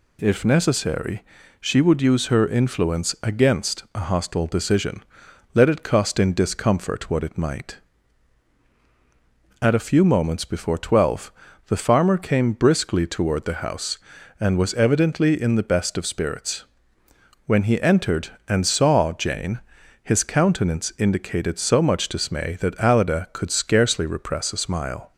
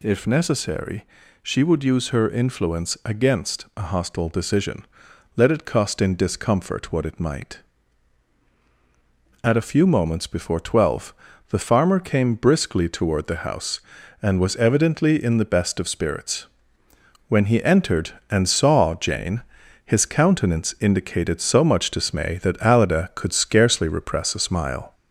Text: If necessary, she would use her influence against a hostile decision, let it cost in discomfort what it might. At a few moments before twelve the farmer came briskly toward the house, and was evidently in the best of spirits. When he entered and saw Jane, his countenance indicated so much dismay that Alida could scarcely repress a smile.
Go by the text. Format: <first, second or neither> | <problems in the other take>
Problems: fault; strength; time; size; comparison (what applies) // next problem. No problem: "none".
first | gets louder; slight; throughout; 3 dB // pauses between "twelve" and "the"; slight; at 11.1 s; 0.36 s long; slight in the first